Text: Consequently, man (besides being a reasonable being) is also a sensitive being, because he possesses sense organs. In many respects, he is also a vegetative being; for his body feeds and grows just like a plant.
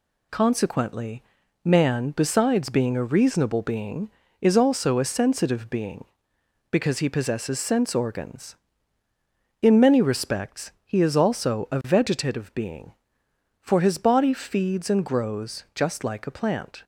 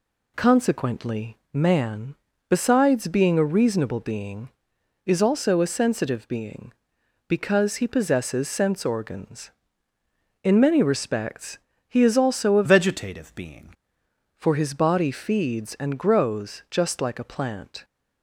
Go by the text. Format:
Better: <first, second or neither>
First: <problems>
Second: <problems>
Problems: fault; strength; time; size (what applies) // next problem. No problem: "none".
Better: first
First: none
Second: changes voice from "vegetative" to "being"; from 12.6 to 13.7 s; 1.1 s long